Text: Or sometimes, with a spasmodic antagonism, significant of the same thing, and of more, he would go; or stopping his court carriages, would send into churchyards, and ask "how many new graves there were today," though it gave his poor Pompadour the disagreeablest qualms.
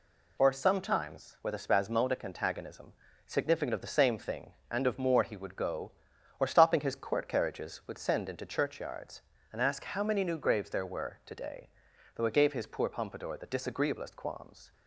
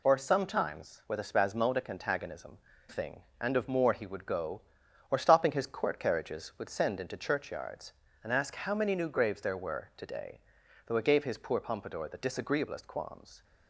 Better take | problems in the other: first | skips "significant of the same"; at 2.7 s

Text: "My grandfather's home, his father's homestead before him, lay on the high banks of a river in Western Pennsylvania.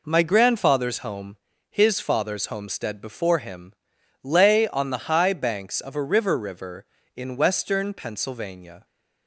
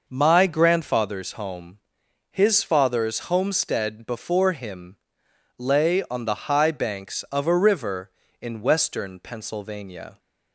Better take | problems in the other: second | says "river" twice; at 6.3 s

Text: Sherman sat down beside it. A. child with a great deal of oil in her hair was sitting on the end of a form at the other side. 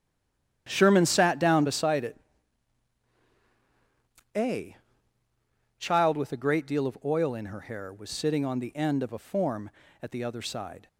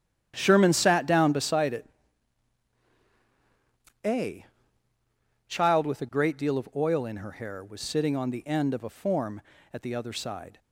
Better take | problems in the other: second | stays silent before the first word; slight; until 0.6 s; 0.6 s long // starts louder than the rest; strong; until 1.6 s; 10.5 dB; strong in the second

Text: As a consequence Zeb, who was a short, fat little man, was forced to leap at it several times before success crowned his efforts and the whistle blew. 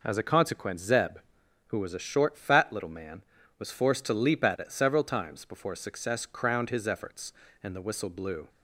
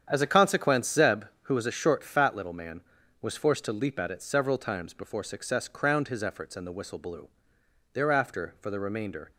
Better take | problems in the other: first | starts louder than the rest; strong; until 1.1 s; 8.5 dB // goes on to say "Thereafter for the remainder"; from 7.9 s on; 1.3 s long

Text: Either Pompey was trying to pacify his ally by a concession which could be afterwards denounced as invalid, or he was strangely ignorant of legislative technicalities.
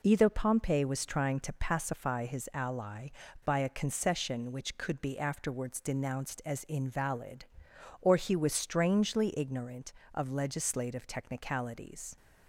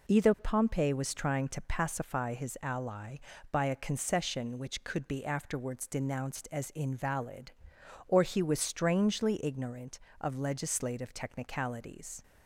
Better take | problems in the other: neither | none

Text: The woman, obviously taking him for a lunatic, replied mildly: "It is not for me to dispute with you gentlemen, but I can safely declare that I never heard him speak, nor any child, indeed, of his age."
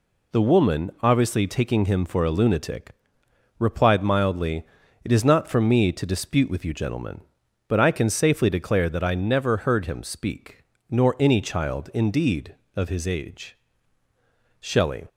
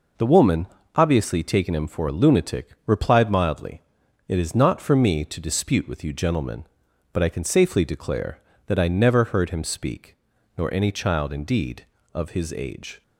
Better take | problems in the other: second | goes on to say "Shelley"; slight; from 14.5 s on; 0.46 s long

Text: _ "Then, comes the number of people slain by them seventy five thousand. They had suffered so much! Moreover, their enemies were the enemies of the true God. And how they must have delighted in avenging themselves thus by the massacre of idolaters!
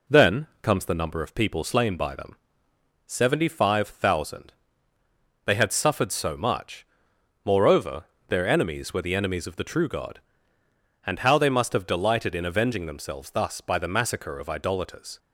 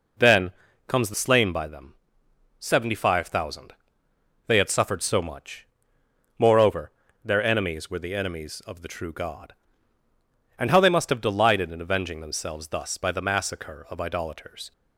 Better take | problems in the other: first | skips "number of people"; at 1.1 s // pauses between "them" and "seventy"; noticeable; at 1.9 s; 0.66 s long; noticeable in the first

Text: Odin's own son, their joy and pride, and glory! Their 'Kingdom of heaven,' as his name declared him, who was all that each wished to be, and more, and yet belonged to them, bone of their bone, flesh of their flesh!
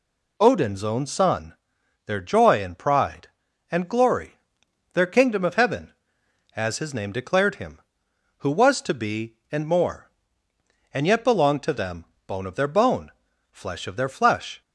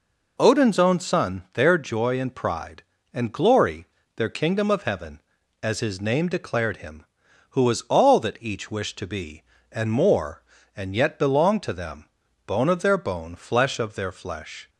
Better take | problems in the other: second | skips "all that each wished"; at 8.8 s

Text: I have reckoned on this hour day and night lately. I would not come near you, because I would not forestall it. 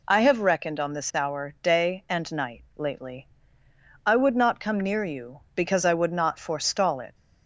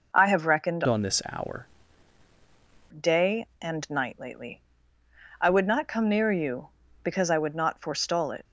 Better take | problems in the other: first | changes voice from "on" to "hour"; from 0.8 to 1.6 s; 0.8 s long

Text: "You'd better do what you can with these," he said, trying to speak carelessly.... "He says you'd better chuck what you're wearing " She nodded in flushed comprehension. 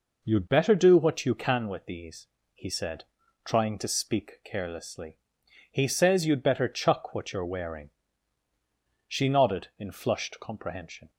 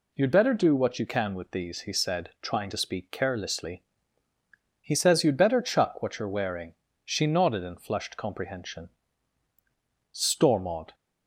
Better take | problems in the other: first | goes on to say "Stormont"; noticeable; from 10.1 s on; 0.84 s long

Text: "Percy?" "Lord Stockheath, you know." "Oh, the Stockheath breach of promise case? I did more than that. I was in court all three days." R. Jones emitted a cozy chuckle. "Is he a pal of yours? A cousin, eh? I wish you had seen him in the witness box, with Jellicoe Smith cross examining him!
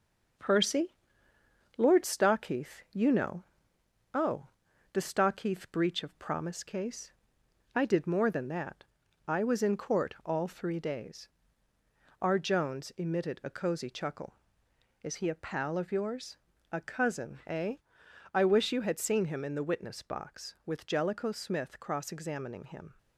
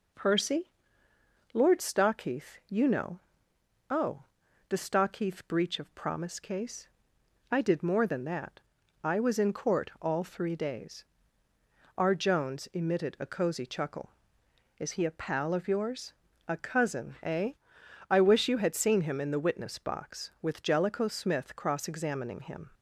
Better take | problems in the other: second | gets quieter; throughout; 3.5 dB

